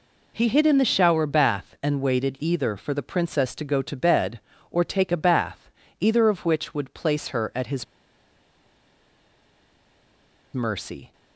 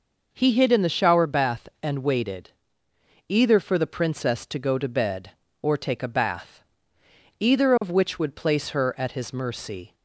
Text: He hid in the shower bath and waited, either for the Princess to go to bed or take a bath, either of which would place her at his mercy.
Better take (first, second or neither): second